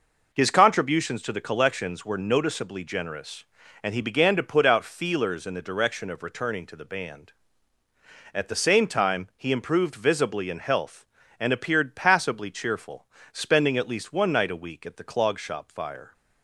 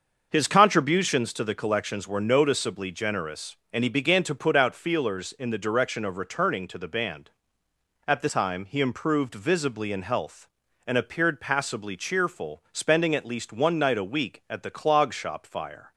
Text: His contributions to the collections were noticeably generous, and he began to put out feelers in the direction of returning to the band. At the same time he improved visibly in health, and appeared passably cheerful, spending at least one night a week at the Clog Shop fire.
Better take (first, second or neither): first